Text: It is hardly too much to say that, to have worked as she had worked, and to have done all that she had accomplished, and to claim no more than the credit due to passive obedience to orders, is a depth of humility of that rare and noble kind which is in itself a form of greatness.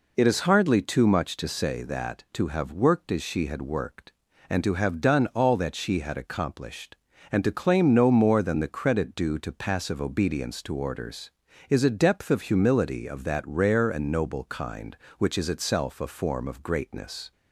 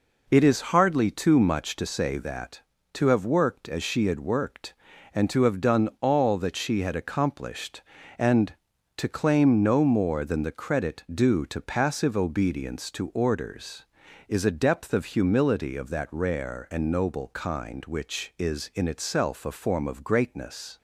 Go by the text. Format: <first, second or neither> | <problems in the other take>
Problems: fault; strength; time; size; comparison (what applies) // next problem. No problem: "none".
second | skips "in"; at 15.4 s